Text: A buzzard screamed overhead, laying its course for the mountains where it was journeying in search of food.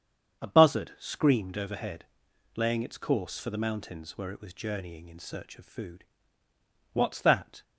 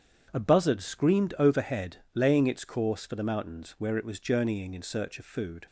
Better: second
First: starts louder than the rest; strong; until 1.4 s; 7.5 dB // goes on to say "What's that"; noticeable; from 6.9 s on; 0.70 s long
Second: starts louder than the rest; strong; until 1.3 s; 8 dB

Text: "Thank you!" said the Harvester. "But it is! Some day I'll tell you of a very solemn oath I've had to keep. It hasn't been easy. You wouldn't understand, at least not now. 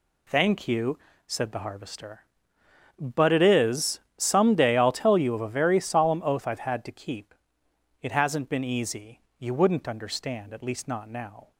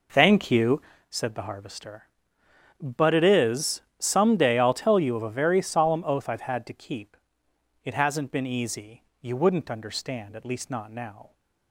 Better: first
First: none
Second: starts louder than the rest; noticeable; until 1.1 s; 4 dB

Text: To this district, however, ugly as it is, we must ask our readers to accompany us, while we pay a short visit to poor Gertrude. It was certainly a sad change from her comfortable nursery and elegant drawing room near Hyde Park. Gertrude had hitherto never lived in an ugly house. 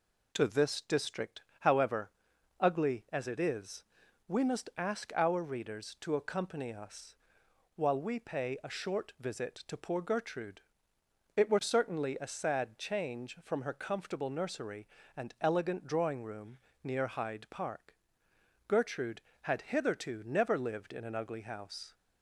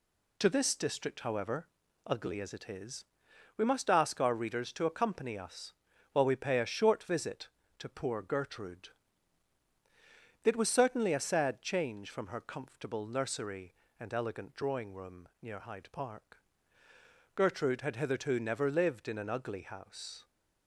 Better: second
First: says "were" for "was"; at 11.4 s // pauses between "room" and "near"; slight; at 16.5 s; 0.26 s long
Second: none

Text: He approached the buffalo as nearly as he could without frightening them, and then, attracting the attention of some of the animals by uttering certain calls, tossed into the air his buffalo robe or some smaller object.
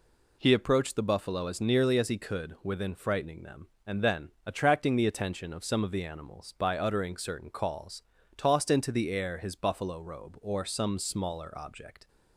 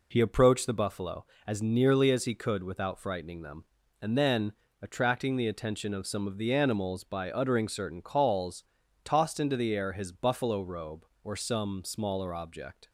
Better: second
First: says "within" for "without"; at 2.6 s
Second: none

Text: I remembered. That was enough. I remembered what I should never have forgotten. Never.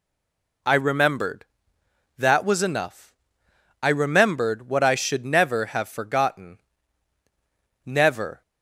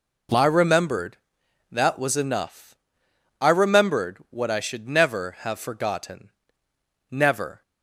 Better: second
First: stays silent before the first word; slight; until 0.6 s; 0.6 s long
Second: none

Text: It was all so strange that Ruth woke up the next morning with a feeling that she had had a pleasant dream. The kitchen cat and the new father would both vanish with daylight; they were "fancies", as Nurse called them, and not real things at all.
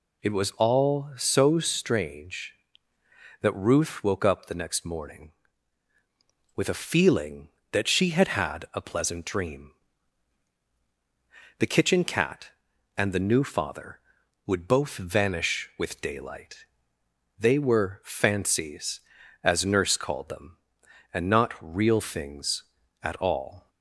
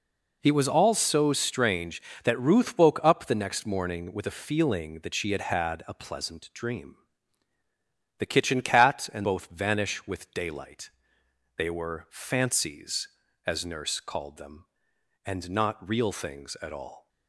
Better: first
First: none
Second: skips "the new father would"; at 9.2 s

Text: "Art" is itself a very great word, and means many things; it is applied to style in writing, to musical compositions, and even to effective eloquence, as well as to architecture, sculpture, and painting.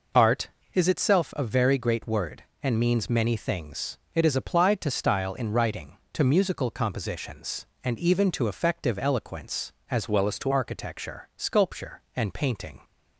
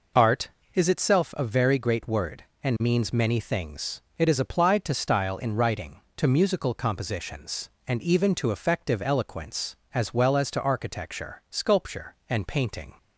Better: second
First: changes voice from "well" to "to"; from 10.0 to 10.5 s; 0.5 s long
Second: none

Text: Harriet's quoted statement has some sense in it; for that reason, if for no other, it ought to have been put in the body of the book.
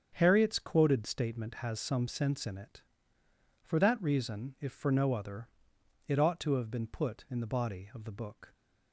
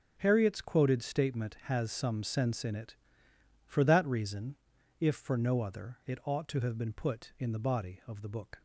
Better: neither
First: starts louder than the rest; strong; until 1.1 s; 7.5 dB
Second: starts louder than the rest; until 1.1 s; 7 dB

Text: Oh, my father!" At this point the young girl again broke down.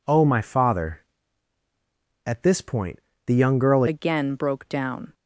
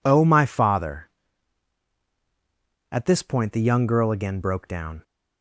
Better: second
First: pauses between "point" and "the"; slight; at 2.9 s; 0.28 s long // changes voice at "again"; from 3.8 s on; 1.3 s long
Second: none

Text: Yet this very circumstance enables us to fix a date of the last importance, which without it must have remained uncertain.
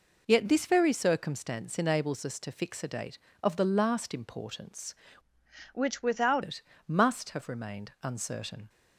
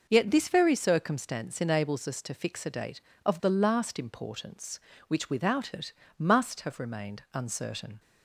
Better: second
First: changes voice from "which" to "without"; from 5.7 to 6.4 s; 0.7 s long // pauses between "it" and "must"; slight; at 6.6 s; 0.26 s long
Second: pauses between "it" and "must"; slight; at 5.9 s; 0.26 s long

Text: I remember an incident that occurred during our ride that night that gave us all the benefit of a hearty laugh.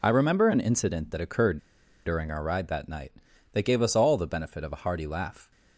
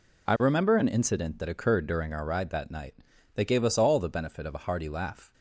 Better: second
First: pauses between "occurred" and "during"; noticeable; at 1.5 s; 0.46 s long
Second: none

